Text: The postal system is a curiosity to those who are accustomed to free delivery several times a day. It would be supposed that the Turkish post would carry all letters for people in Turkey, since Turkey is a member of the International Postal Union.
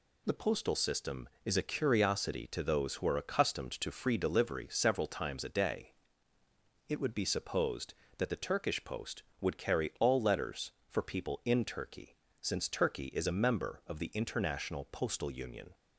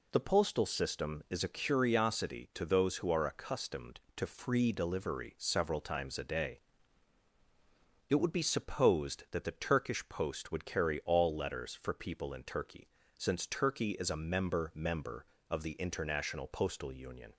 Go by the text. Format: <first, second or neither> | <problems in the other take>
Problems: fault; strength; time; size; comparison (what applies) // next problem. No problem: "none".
first | says "member" twice; at 14.7 s